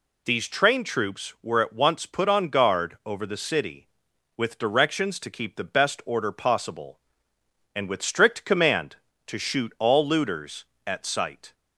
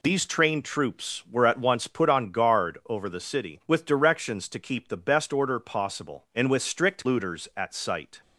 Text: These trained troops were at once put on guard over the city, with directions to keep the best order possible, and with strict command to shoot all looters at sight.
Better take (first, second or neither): first